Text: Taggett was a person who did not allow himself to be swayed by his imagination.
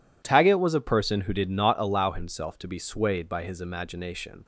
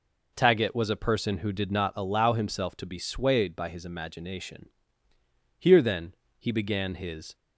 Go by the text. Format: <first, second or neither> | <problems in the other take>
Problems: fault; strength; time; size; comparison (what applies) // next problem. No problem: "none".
first | goes on to say "Here then he began his"; strong; from 5.5 s on; 1.7 s long